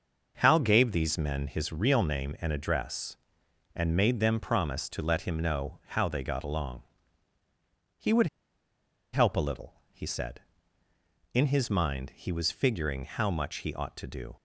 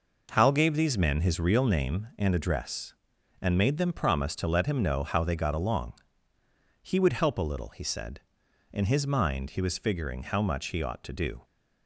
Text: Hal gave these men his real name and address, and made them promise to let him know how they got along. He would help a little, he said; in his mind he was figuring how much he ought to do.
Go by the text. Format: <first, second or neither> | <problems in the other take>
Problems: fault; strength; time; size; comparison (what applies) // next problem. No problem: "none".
second | starts louder than the rest; until 1.4 s; 6 dB // pauses between "would" and "help"; noticeable; at 8.2 s; 0.87 s long